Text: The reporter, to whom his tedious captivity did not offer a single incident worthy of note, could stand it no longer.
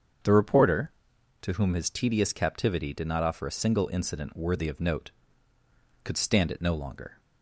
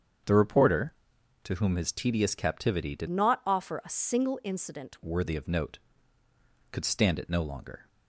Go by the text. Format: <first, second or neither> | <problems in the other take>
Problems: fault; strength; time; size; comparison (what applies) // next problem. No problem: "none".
first | starts louder than the rest; strong; until 1.7 s; 7.5 dB; also in the first // changes voice from "not" to "incident"; from 3.0 to 4.9 s; 1.9 s long